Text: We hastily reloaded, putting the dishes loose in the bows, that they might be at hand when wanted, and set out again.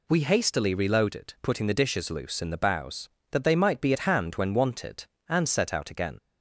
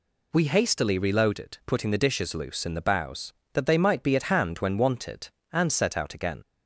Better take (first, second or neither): neither